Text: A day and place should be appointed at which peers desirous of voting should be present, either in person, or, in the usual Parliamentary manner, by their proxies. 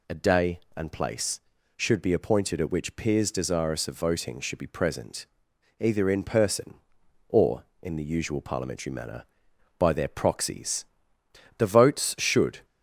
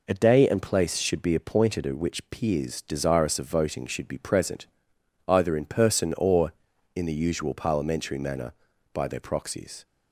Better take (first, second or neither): second